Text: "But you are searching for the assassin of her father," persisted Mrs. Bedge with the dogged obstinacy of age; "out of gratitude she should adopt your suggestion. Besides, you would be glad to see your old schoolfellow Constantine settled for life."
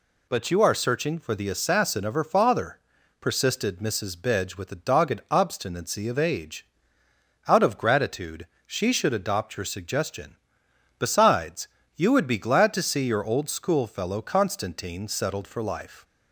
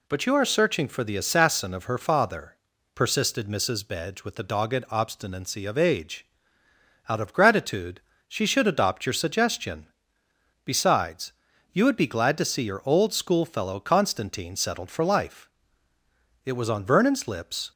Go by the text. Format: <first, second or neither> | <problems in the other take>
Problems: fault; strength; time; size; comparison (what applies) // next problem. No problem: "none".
first | pauses between "gratitude" and "she"; slight; at 8.0 s; 0.26 s long; slight in the first // goes on to say "It was on Vernon's lips"; noticeable; from 16.4 s on; 1.2 s long